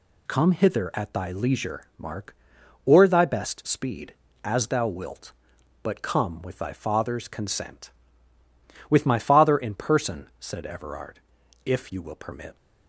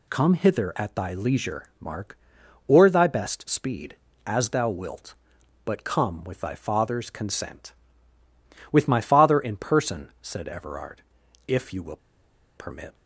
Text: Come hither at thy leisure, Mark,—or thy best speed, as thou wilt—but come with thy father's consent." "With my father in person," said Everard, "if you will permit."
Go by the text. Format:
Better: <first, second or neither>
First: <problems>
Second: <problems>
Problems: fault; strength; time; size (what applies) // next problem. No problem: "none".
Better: first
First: none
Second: pauses between "will" and "permit"; noticeable; at 11.9 s; 0.60 s long